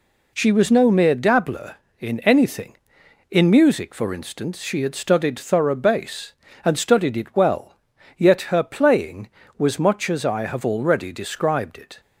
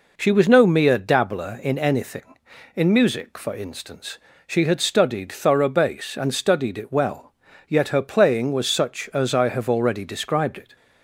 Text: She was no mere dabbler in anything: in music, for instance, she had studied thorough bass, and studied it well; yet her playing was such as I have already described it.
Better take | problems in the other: second | says "much" for "such"; at 9.7 s

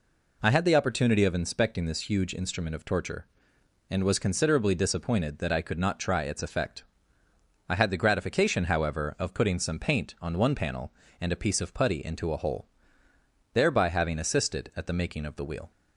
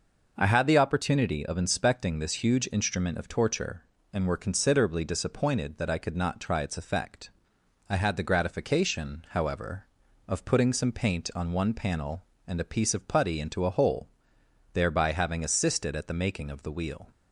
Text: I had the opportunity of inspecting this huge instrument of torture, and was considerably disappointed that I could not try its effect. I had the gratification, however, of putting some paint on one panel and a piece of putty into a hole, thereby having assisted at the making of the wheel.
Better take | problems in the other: first | says "were" for "was"; at 4.2 s

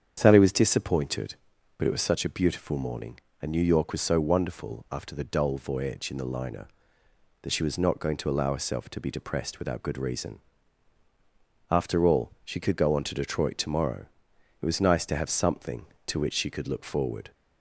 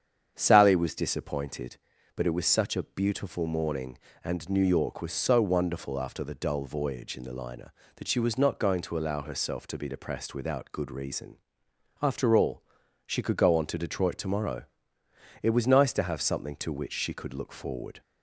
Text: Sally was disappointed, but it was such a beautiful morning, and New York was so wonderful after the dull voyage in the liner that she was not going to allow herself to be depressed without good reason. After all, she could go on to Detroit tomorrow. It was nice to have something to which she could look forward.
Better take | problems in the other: neither | starts louder than the rest; strong; the same in both

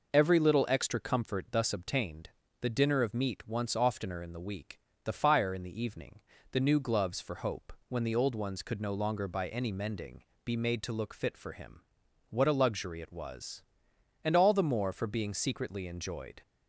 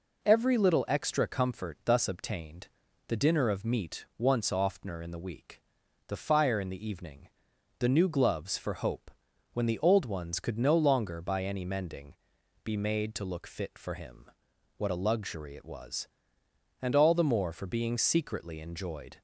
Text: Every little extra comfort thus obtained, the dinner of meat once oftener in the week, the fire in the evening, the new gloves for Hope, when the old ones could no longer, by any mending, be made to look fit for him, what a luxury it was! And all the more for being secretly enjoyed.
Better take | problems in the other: neither | none

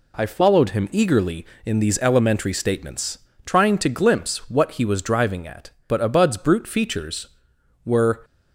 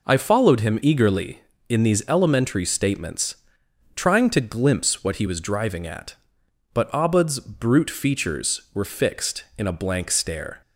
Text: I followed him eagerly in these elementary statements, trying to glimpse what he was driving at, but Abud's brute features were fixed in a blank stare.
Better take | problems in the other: second | stops before "fixed in a blank stare"; at 8.2 s

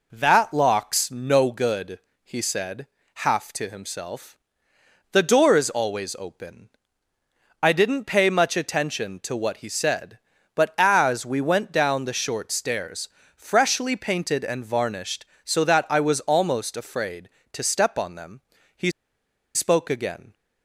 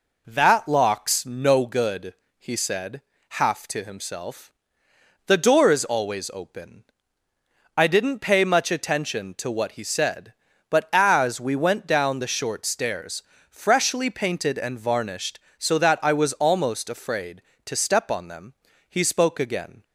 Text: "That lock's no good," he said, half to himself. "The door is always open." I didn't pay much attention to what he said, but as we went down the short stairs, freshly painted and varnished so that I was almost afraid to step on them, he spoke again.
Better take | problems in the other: second | pauses between "he" and "spoke"; noticeable; at 18.8 s; 0.64 s long

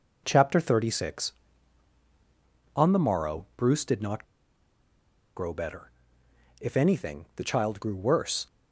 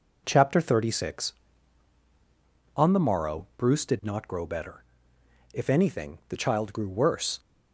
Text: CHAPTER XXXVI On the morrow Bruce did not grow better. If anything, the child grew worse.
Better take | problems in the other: second | pauses between "not" and "grow"; at 4.2 s; 1.1 s long

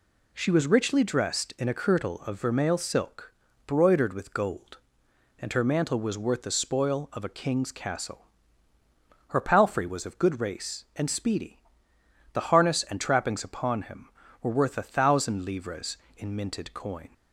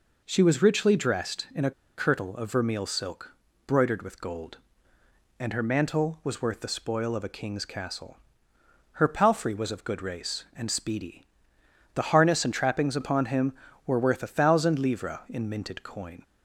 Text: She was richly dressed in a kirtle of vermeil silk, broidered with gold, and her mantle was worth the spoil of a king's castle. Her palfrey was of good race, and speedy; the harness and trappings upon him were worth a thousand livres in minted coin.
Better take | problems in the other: first | pauses between "a" and "kirtle"; slight; at 1.7 s; 0.26 s long

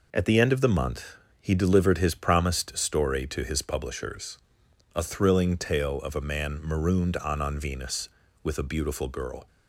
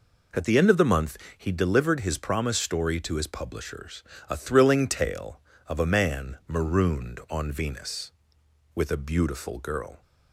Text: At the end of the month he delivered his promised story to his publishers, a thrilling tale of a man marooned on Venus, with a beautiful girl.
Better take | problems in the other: second | pauses between "month" and "he"; slight; at 1.1 s; 0.24 s long; slight in the second // says "on" twice; at 7.4 s

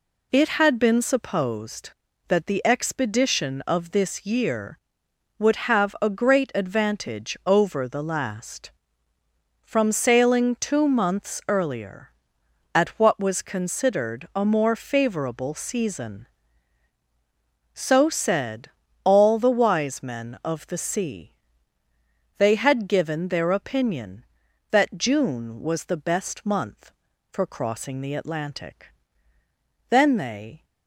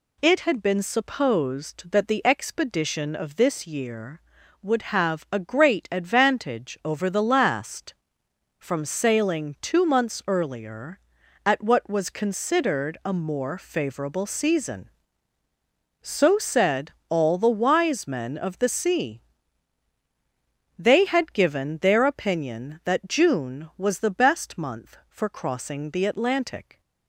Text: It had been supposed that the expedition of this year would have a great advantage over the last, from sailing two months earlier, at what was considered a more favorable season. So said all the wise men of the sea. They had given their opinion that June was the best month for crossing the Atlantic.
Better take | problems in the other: second | pauses between "said" and "all"; slight; at 18.6 s; 0.36 s long; slight in the second // goes on to say "Then they"; noticeable; from 29.8 s on; 0.74 s long

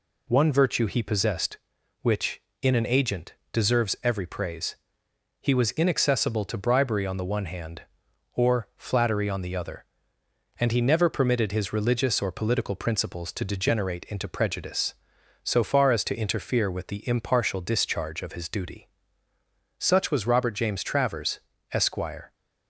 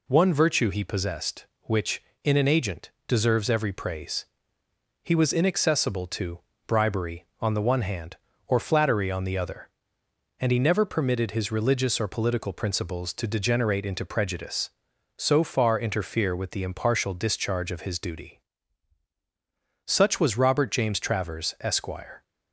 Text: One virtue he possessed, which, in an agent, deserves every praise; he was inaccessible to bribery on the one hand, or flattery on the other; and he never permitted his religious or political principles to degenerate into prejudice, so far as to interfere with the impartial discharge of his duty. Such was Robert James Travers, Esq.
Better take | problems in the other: first | pauses between "to" and "bribery"; slight; at 6.4 s; 0.26 s long // skips "as to"; at 15.7 s

